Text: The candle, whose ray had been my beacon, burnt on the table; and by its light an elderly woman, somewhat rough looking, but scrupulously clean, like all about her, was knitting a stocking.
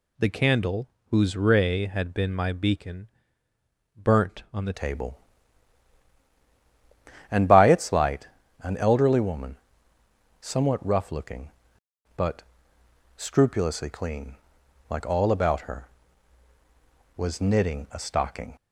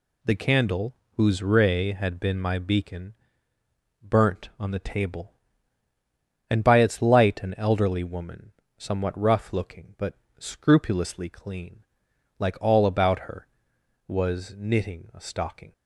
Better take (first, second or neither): second